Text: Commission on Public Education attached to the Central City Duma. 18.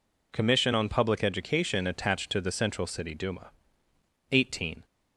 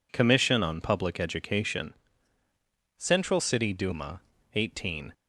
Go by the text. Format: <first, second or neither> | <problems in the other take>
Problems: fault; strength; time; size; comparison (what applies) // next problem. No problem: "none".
first | skips "attached to the"; at 2.4 s